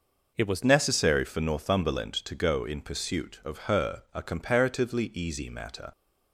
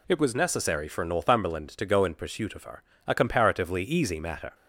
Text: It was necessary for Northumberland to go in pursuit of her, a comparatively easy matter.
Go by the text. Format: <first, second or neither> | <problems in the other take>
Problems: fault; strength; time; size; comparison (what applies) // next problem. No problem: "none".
second | changes voice at "necessary"; from 0.6 s on; 5.3 s long